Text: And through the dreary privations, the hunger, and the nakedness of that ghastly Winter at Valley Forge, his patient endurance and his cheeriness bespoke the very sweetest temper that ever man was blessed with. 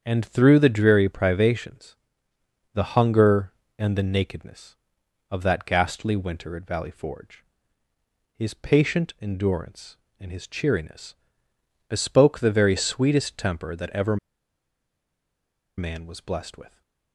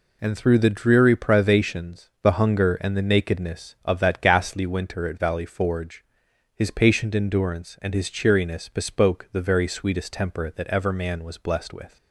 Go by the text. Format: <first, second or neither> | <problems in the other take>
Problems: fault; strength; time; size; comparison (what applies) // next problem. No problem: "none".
second | starts louder than the rest; strong; until 1.0 s; 7.5 dB // pauses between "cheeriness" and "bespoke"; noticeable; at 11.1 s; 0.72 s long // pauses between "ever" and "man"; strong; at 14.1 s; 1.6 s long